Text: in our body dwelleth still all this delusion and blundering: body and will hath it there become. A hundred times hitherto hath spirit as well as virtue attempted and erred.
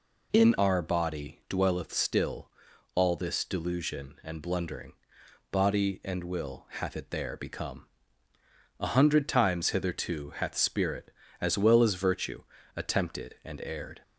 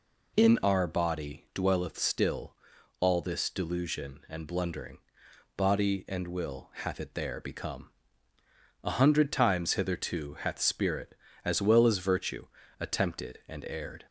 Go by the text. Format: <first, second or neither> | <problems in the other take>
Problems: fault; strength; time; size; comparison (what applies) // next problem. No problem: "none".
neither | pauses between "still" and "all"; the same in both // pauses between "virtue" and "attempted"; slight; the same in both